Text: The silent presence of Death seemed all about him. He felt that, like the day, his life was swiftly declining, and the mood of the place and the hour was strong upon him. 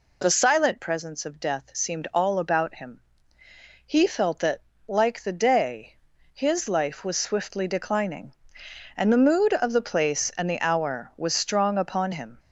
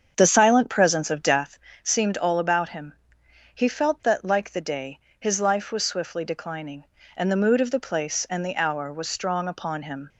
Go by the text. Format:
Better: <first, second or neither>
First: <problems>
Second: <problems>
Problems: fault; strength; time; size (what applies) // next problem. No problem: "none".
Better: first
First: none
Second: starts louder than the rest; strong; until 1.6 s; 7.5 dB // pauses between "Death" and "seemed"; slight; at 1.5 s; 0.24 s long